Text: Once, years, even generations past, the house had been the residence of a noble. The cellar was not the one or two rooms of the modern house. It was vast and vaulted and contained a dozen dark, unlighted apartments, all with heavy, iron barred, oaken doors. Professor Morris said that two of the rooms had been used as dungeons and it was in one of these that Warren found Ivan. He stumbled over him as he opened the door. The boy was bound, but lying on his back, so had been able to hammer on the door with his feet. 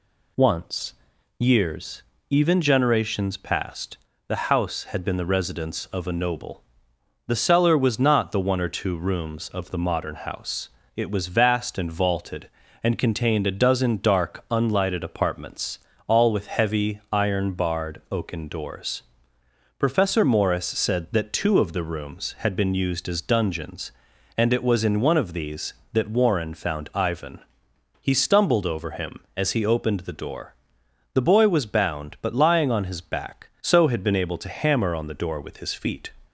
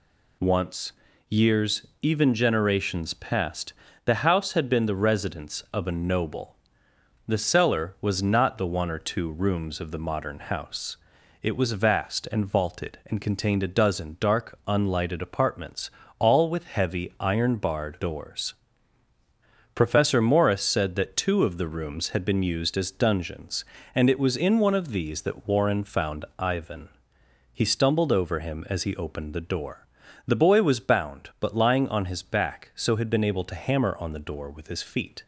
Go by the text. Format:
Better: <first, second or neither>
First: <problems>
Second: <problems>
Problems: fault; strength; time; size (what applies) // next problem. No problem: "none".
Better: first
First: none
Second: skips "oaken"; at 17.9 s